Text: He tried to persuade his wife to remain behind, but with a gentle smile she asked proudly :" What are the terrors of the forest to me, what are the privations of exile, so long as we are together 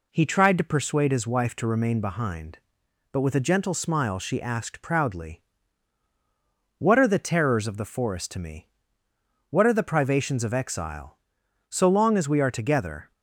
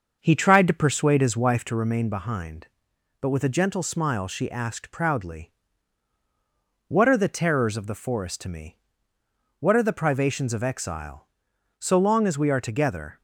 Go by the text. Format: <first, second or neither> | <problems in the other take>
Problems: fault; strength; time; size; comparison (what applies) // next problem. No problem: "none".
first | starts louder than the rest; until 1.7 s; 6.5 dB